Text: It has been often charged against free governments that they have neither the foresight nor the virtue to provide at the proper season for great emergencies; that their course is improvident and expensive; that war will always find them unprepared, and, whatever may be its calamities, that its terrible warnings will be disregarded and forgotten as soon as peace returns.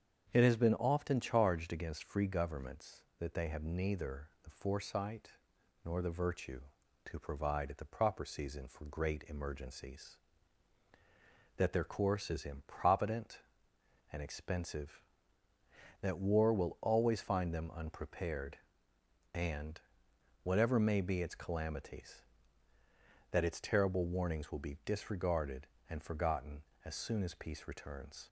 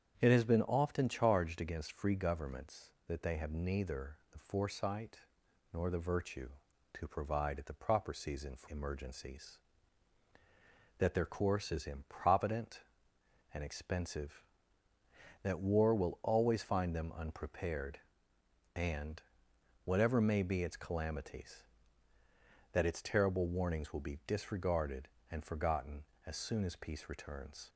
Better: first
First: starts louder than the rest; strong; until 1.3 s; 7.5 dB // pauses between "neither" and "the"; slight; at 4.2 s; 0.16 s long // pauses between "foresight" and "nor"; noticeable; at 5.2 s; 0.56 s long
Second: starts louder than the rest; strong; until 1.2 s; 8 dB // pauses between "neither" and "the"; slight; at 4.1 s; 0.16 s long // pauses between "foresight" and "nor"; noticeable; at 5.1 s; 0.56 s long // skips "great"; at 8.6 s

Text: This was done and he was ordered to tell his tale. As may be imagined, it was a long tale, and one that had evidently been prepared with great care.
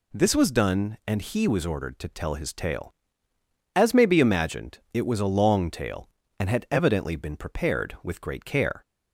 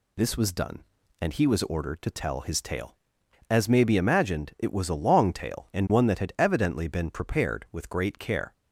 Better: second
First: skips "one that"; at 6.4 s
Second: none

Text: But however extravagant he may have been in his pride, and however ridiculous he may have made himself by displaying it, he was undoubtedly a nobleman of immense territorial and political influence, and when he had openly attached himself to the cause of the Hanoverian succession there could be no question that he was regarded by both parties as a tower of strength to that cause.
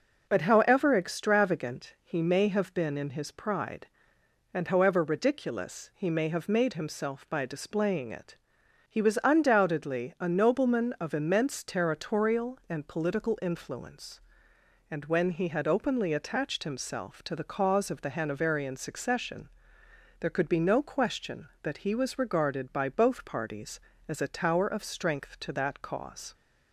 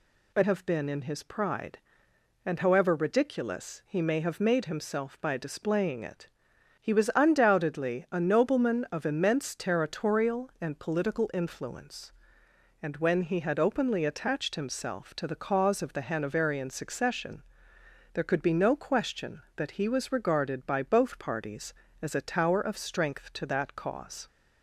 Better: first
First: pauses between "succession" and "there"; noticeable; at 19.4 s; 0.72 s long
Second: skips "however extravagant he may"; at 0.4 s // pauses between "succession" and "there"; noticeable; at 17.4 s; 0.72 s long

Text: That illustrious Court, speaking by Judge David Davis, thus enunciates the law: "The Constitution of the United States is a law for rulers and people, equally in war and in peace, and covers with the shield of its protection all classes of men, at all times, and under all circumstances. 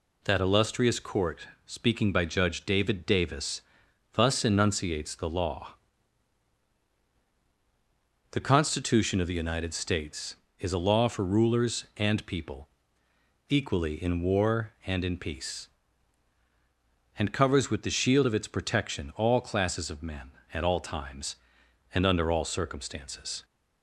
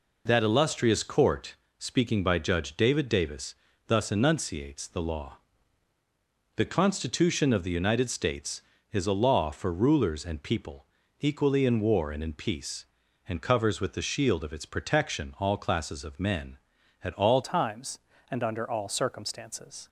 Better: first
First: none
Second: changes voice at "times"; from 17.4 s on; 2.4 s long

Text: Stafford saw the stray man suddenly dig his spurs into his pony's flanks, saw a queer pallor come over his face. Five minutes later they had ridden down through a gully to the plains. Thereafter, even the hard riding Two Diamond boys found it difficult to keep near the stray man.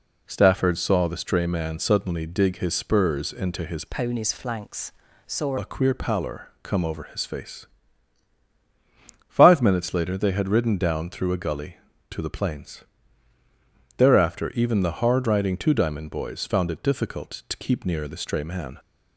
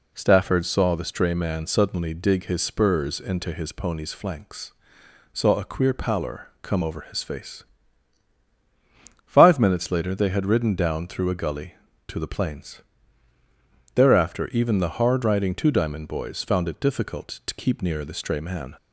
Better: second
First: changes voice from "pony's" to "saw"; from 3.8 to 5.5 s; 1.7 s long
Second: none

